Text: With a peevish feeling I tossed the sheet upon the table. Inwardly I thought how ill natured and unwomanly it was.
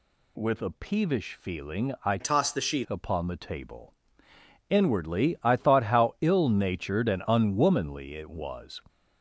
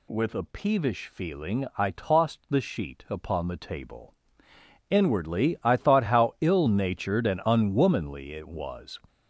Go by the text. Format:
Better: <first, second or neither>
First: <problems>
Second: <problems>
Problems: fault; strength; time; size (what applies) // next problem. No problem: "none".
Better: second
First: changes voice from "tossed" to "sheet"; from 2.1 to 2.8 s; 0.7 s long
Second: none